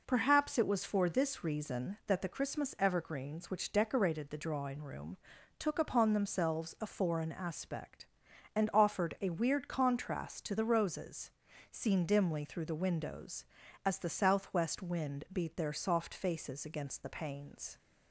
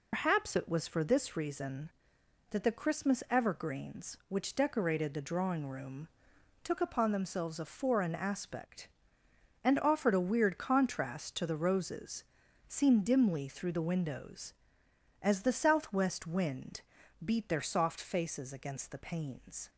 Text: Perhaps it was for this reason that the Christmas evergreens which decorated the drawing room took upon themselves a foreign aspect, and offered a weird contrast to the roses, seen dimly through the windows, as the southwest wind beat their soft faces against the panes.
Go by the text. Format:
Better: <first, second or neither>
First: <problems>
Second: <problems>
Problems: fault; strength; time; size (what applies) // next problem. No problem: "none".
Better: first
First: pauses between "room" and "took"; at 5.1 s; 0.42 s long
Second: loses the start of "Perhaps"; at 0.1 s; 125 ms // pauses between "room" and "took"; noticeable; at 6.0 s; 0.56 s long // pauses between "wind" and "beat"; at 16.8 s; 0.42 s long